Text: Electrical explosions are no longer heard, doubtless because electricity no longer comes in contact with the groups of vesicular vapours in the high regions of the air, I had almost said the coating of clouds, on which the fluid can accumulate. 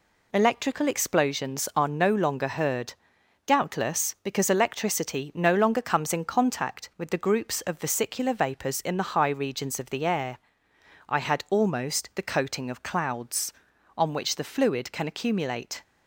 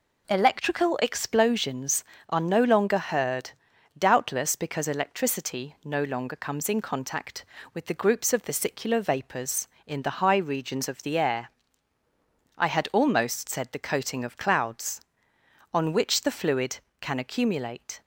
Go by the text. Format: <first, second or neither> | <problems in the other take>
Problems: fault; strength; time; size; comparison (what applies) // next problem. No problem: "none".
second | skips "said"; at 12.1 s